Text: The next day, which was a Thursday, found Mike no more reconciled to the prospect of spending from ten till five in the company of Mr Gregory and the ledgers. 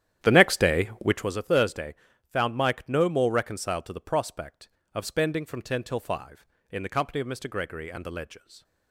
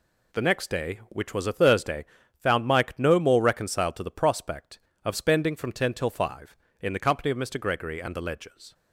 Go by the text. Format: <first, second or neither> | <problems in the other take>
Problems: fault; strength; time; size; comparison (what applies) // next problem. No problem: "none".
second | starts louder than the rest; strong; until 1.4 s; 11 dB